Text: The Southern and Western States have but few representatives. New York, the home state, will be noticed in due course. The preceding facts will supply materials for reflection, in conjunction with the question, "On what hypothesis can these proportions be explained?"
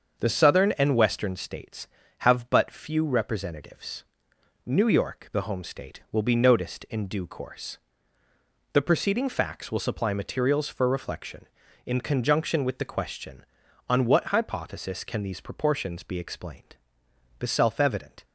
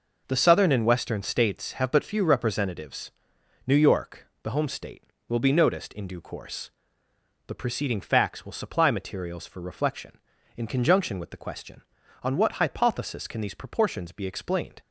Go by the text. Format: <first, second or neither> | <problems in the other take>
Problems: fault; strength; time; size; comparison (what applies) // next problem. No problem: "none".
second | starts louder than the rest; until 1.2 s; 6.5 dB // goes on to say "The self evident"; noticeable; from 17.3 s on; 0.86 s long